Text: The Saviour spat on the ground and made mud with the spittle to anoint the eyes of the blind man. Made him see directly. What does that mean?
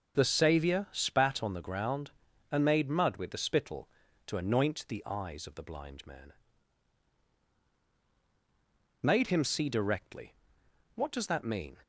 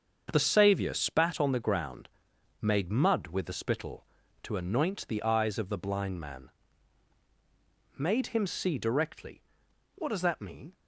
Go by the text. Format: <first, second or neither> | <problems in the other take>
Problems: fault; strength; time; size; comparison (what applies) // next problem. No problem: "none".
first | starts louder than the rest; until 1.3 s; 7 dB; also in the first // skips "and"; at 2.3 s